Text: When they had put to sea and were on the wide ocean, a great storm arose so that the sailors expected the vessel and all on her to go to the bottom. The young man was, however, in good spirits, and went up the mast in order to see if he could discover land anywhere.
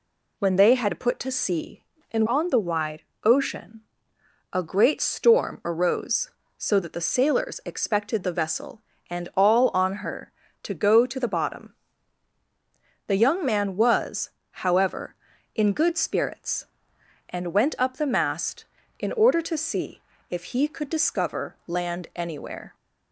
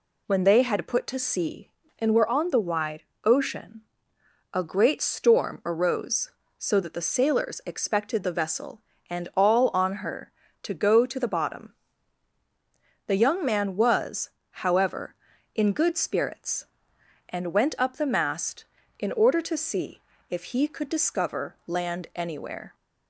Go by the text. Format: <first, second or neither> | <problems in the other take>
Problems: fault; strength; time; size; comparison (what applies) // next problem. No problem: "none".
second | skips "were"; at 2.2 s // pauses between "wide" and "ocean"; slight; at 3.0 s; 0.22 s long; slight in the second // pauses between "see" and "if"; slight; at 20.0 s; 0.30 s long; slight in the second